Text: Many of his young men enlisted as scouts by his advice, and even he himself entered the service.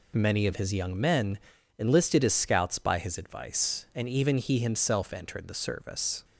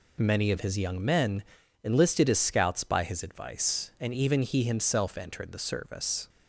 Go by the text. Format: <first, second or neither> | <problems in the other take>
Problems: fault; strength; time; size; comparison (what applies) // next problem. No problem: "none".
neither | pauses between "men" and "enlisted"; the same in both